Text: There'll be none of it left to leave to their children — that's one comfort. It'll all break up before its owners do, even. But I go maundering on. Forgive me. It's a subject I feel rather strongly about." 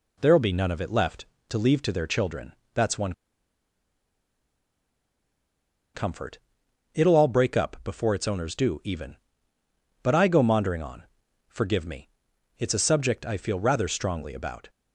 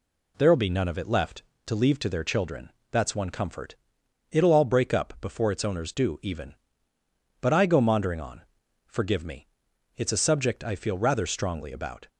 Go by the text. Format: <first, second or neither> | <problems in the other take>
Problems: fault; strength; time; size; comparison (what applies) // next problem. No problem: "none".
second | pauses between "one" and "comfort"; strong; at 3.1 s; 2.8 s long